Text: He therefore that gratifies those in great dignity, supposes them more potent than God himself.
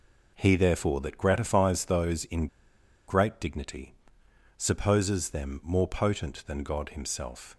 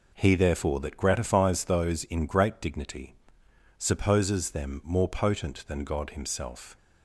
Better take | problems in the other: second | pauses between "in" and "great"; noticeable; at 2.4 s; 0.60 s long

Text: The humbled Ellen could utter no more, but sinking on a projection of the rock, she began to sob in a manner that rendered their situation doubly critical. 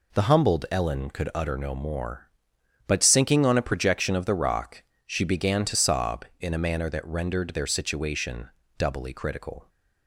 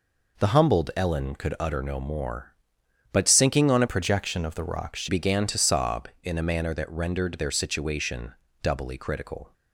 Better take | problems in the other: first | changes voice from "projection" to "she"; from 3.8 to 5.0 s; 1.2 s long // pauses between "situation" and "doubly"; slight; at 8.3 s; 0.30 s long; slight in the first

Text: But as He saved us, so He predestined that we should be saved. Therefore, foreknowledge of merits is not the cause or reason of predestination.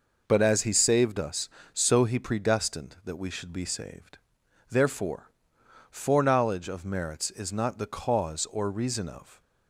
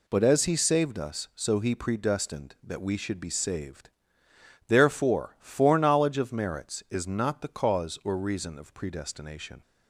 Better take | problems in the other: second | stops before "predestination"; at 9.4 s

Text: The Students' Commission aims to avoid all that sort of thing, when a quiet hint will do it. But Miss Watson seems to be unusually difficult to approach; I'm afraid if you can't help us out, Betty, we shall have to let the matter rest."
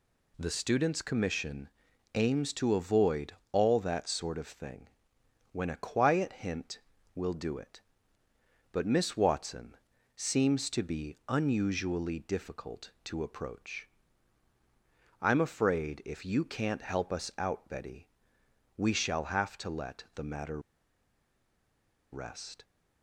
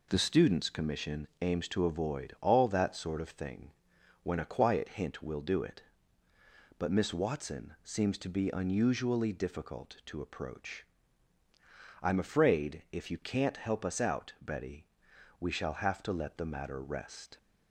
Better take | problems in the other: second | pauses between "Commission" and "aims"; at 1.6 s; 0.44 s long // pauses between "avoid" and "all"; slight; at 3.3 s; 0.22 s long // pauses between "Watson" and "seems"; at 9.7 s; 0.40 s long // pauses between "matter" and "rest"; strong; at 20.5 s; 1.5 s long

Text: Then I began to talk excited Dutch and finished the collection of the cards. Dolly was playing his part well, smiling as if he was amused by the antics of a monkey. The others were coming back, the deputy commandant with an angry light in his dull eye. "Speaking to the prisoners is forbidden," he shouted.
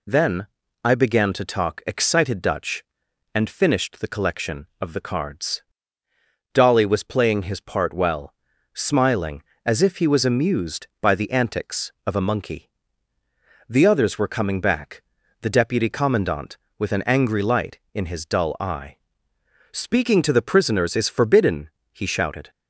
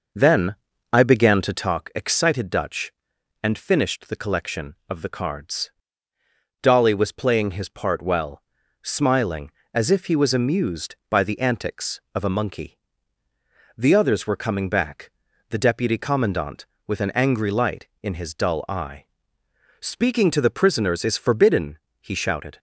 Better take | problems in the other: first | starts louder than the rest; noticeable; until 1.7 s; 5.5 dB // pauses between "Then" and "I"; at 0.5 s; 0.38 s long; also in the first

